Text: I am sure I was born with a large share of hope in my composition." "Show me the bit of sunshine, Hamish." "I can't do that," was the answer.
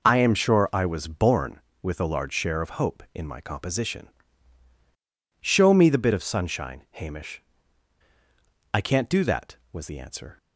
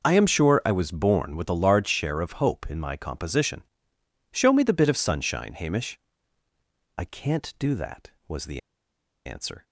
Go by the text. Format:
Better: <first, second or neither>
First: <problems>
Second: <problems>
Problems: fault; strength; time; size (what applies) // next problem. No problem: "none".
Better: first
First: none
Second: pauses between "the" and "answer"; noticeable; at 8.5 s; 0.65 s long